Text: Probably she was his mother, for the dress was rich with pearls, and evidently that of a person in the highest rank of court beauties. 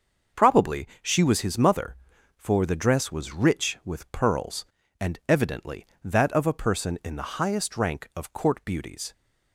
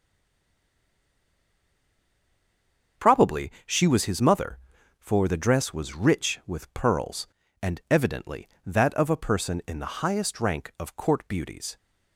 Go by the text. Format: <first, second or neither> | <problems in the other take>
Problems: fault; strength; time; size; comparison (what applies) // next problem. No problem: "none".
first | stays silent before the first word; strong; until 2.9 s; 2.9 s long // starts louder than the rest; until 4.1 s; 6.5 dB; also in the first // pauses between "Probably" and "she"; slight; at 3.5 s; 0.16 s long; slight in the first